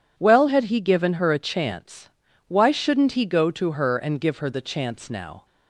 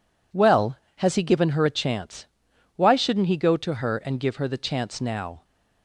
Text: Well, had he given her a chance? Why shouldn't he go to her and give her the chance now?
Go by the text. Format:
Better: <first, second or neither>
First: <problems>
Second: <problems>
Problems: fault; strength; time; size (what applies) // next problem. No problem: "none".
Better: first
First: none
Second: says "has" for "had"; at 0.9 s